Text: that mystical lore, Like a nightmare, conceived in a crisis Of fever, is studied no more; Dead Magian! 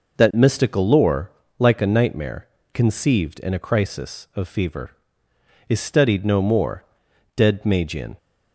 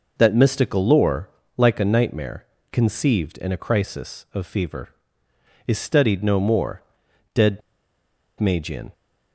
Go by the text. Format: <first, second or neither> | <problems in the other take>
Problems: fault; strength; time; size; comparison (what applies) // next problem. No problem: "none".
first | pauses between "Dead" and "Magian"; noticeable; at 7.6 s; 0.79 s long